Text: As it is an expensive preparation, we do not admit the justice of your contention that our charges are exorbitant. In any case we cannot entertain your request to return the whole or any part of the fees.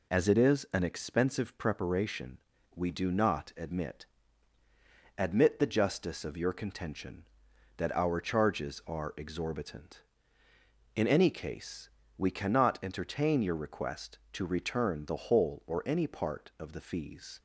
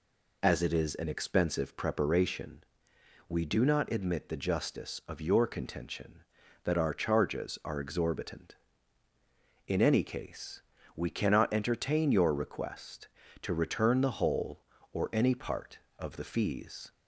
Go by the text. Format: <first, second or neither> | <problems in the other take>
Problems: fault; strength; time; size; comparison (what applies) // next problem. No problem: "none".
second | says "admit" twice; at 5.1 s // pauses between "case" and "we"; slight; at 11.8 s; 0.30 s long; slight in the second